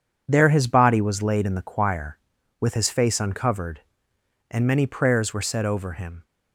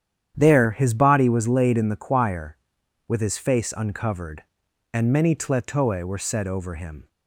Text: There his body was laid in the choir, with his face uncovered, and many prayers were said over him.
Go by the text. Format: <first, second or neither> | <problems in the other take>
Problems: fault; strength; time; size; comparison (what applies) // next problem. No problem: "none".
first | starts louder than the rest; strong; until 1.3 s; 9.5 dB // says "tletoe" for "prayers"; at 5.3 s